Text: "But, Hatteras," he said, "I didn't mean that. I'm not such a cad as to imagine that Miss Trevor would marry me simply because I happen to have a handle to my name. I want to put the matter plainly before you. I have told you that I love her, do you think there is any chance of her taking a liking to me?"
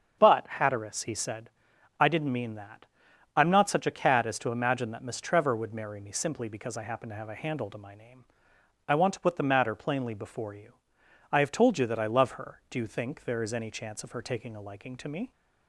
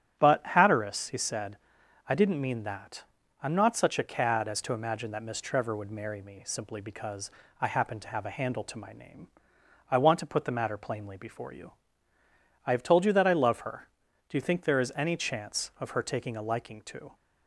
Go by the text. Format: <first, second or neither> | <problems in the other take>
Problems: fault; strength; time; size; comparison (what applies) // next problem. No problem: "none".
first | starts louder than the rest; strong; until 1.2 s; 9 dB; strong in the first // pauses between "because" and "I"; slight; at 7.3 s; 0.28 s long // stops before "me"; at 17.1 s